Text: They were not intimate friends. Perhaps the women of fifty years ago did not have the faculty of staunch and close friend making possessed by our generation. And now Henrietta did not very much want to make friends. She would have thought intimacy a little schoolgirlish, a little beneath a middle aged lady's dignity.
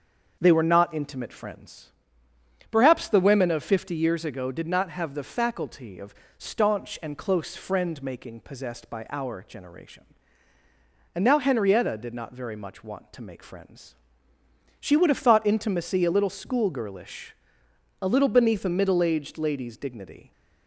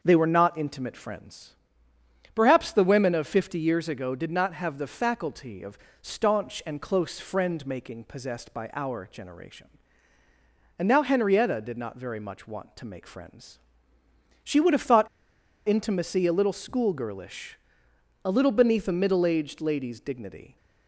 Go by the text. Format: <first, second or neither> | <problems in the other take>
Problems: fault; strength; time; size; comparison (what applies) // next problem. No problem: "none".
first | starts louder than the rest; until 1.0 s; 6.5 dB; also in the first // pauses between "of" and "staunch"; slight; at 5.7 s; 0.24 s long; slight in the first // pauses between "thought" and "intimacy"; noticeable; at 15.0 s; 0.59 s long